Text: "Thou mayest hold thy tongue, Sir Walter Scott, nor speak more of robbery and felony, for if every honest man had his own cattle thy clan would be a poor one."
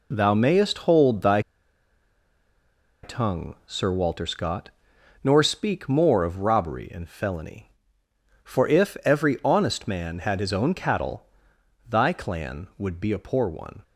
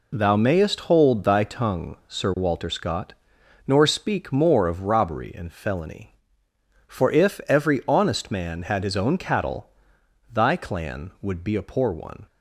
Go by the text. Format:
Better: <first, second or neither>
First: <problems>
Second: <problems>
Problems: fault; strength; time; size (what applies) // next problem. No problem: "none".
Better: second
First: pauses between "thy" and "tongue"; strong; at 1.3 s; 1.6 s long // pauses between "cattle" and "thy"; noticeable; at 11.2 s; 0.64 s long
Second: pauses between "cattle" and "thy"; noticeable; at 9.6 s; 0.64 s long